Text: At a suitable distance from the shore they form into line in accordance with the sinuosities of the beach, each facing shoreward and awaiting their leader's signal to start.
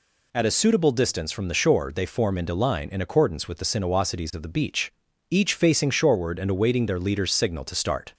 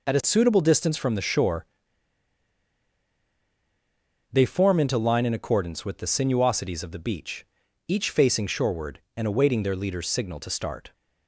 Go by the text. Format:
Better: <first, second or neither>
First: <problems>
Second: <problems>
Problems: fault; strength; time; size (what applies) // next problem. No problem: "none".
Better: first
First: none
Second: pauses between "shore" and "they"; strong; at 1.6 s; 2.6 s long